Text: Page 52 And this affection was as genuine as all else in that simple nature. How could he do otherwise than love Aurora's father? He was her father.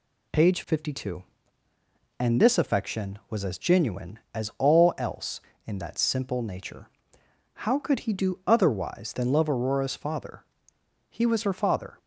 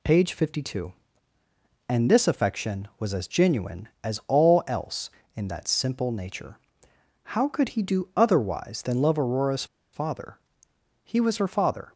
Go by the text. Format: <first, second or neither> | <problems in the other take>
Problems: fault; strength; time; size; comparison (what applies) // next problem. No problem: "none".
first | pauses between "Aurora's" and "father"; slight; at 9.6 s; 0.27 s long